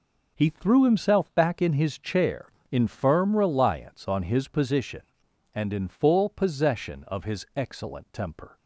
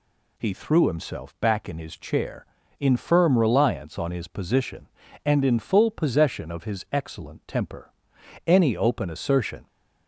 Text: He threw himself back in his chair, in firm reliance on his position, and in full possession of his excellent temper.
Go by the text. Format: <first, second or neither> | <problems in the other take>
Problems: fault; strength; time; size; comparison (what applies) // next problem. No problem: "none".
first | goes on to say "Any open assertion"; noticeable; from 8.4 s on; 1.2 s long